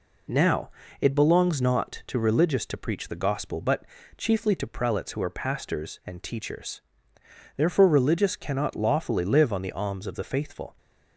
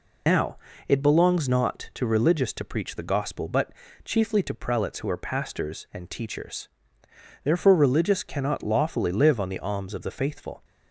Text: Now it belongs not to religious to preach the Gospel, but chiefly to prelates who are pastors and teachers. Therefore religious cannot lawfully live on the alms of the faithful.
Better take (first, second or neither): first